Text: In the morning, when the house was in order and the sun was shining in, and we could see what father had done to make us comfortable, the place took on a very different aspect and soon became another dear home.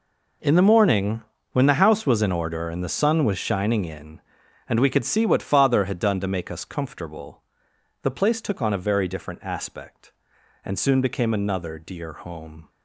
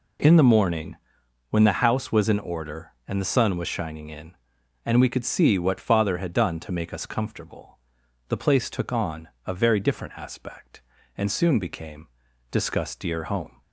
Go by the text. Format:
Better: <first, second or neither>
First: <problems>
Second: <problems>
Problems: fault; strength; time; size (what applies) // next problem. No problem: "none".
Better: first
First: none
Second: pauses between "on" and "a"; slight; at 9.2 s; 0.18 s long // says "discuss" for "another"; at 12.5 s